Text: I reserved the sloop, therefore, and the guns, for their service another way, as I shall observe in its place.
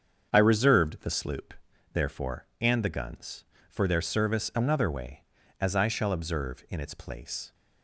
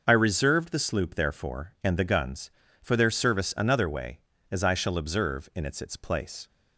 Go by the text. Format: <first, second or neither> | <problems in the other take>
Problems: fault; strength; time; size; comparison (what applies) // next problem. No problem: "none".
first | starts louder than the rest; noticeable; until 1.0 s; 6 dB; strong in the first // says "its" twice; at 5.7 s